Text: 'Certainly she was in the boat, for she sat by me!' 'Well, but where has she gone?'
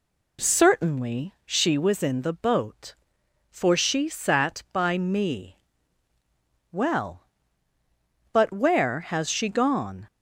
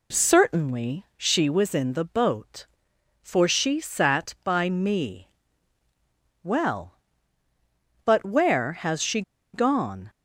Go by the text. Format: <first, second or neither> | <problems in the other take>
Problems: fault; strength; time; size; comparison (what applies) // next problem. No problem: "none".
first | pauses between "she" and "gone"; slight; at 9.2 s; 0.32 s long